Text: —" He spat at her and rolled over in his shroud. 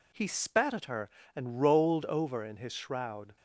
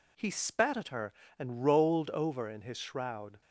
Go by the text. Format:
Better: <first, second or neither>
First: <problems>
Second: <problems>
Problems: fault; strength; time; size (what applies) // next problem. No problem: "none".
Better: neither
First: none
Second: none